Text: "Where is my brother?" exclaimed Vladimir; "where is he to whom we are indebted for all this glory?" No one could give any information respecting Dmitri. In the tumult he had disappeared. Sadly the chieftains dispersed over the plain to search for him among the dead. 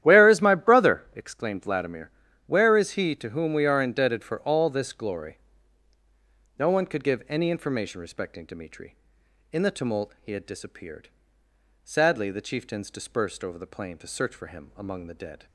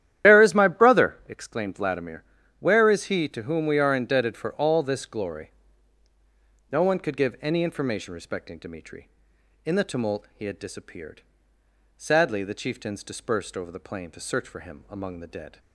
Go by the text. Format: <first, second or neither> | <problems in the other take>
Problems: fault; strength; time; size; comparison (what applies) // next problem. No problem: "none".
first | loses the start of "Where"; at 0.2 s; 85 ms // starts louder than the rest; strong; until 1.3 s; 11.5 dB; strong in the first